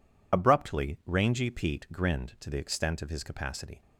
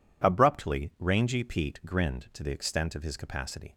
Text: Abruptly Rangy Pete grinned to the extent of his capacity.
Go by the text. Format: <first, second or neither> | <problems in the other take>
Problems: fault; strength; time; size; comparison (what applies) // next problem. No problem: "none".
second | loses the start of "Abruptly"; at 0.3 s; 50 ms